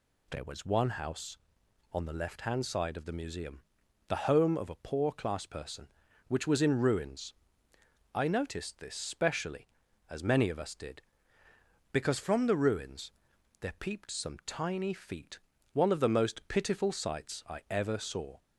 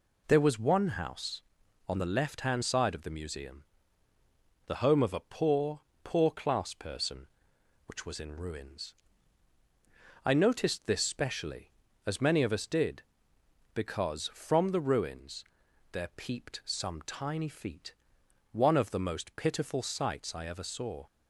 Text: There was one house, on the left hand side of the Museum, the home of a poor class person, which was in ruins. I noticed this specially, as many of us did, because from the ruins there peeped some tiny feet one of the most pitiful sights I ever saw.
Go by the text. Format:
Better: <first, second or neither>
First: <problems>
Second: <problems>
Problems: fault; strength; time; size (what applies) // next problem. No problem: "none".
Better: first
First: pauses between "ruins" and "there"; noticeable; at 13.1 s; 0.50 s long // pauses between "feet" and "one"; slight; at 15.3 s; 0.34 s long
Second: says "poor" twice; at 6.0 s // pauses between "ruins" and "there"; noticeable; at 15.4 s; 0.48 s long // pauses between "feet" and "one"; noticeable; at 17.9 s; 0.56 s long